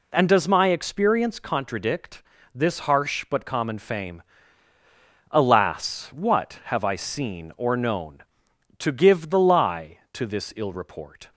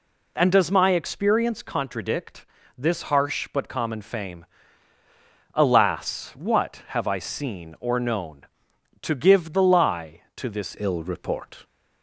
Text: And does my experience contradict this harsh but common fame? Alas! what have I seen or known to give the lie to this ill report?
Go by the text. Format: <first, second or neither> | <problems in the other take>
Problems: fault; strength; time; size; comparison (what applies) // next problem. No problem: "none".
first | pauses between "contradict" and "this"; slight; at 2.4 s; 0.32 s long; slight in the first // changes voice at "ill"; from 10.7 s on; 0.9 s long